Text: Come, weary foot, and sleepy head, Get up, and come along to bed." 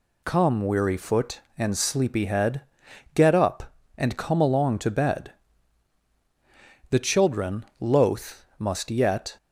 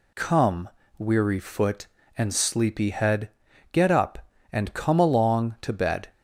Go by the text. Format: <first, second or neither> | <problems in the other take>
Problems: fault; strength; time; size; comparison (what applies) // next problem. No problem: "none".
second | goes on to say "The children loath must yet"; strong; from 6.9 s on; 2.4 s long